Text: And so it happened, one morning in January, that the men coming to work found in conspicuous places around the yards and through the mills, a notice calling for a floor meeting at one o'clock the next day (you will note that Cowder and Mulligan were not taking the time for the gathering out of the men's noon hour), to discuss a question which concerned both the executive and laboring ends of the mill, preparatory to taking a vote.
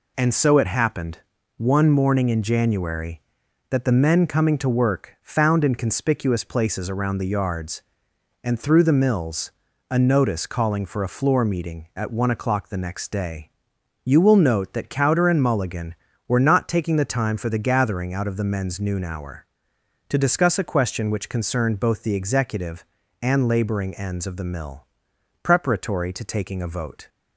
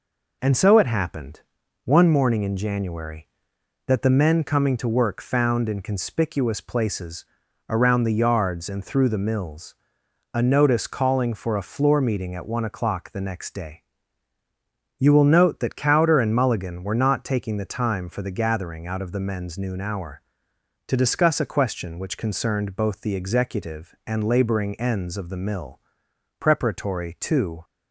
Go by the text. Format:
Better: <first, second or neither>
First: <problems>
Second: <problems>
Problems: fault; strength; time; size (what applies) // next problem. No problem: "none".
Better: first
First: none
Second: pauses between "places" and "around"; at 7.2 s; 0.44 s long // stops before "taking a vote"; at 27.6 s